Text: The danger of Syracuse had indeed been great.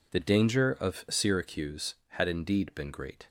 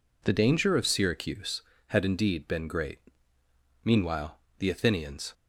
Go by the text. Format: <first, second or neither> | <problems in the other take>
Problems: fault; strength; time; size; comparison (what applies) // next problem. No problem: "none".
first | goes on to say "Meanwhile the Athenians"; from 3.8 s on; 1.5 s long